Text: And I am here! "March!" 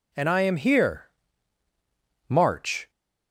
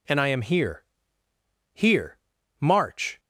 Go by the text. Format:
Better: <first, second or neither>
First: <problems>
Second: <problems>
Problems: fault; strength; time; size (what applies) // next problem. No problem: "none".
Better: first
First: none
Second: says "here" twice; at 1.7 s